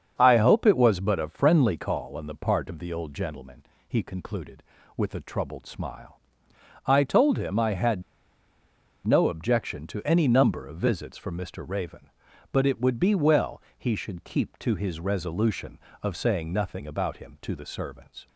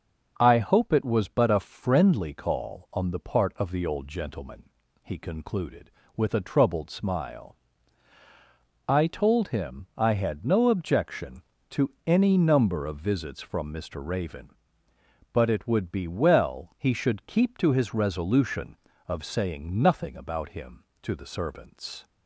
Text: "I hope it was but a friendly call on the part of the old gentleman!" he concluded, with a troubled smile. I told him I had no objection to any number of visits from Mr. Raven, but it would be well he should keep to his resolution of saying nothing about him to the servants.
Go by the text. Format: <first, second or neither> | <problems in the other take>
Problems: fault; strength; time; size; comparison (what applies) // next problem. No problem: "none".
second | starts louder than the rest; until 1.2 s; 7 dB; also in the second // pauses between "had" and "no"; at 8.0 s; 1.0 s long // pauses between "well" and "he"; slight; at 13.6 s; 0.16 s long